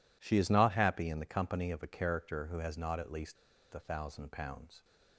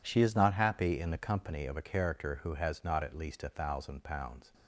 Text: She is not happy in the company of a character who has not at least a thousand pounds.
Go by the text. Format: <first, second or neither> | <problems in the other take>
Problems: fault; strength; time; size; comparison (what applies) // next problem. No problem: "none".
second | pauses between "least" and "a"; at 3.3 s; 0.38 s long